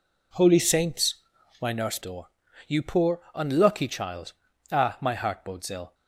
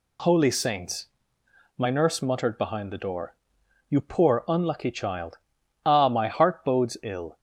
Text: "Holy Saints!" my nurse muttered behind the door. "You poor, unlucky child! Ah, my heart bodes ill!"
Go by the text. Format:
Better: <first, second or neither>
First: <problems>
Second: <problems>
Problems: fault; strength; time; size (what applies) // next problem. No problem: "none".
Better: second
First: skips "muttered behind the"; at 2.0 s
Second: none